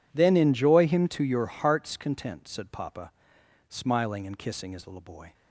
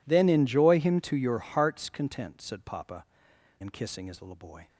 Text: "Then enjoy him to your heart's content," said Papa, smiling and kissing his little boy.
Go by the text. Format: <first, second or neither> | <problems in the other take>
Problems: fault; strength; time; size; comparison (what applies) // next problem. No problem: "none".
first | skips "smiling"; at 3.3 s